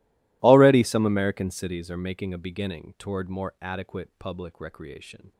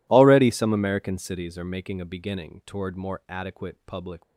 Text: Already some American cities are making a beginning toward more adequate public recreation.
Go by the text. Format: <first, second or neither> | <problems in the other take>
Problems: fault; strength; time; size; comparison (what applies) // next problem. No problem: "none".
first | stops before "recreation"; at 4.2 s